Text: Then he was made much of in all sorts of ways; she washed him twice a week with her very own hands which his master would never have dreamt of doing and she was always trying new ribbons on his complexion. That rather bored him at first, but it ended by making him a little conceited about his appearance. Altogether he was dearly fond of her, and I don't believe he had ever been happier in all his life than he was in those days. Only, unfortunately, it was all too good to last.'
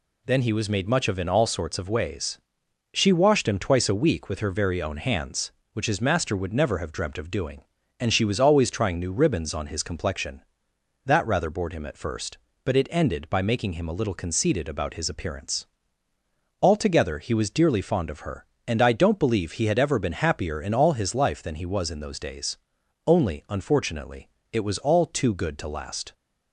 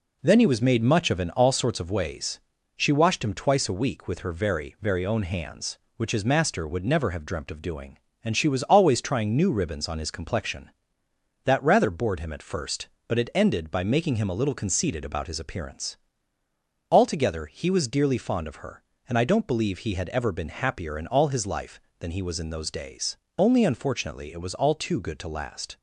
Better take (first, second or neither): first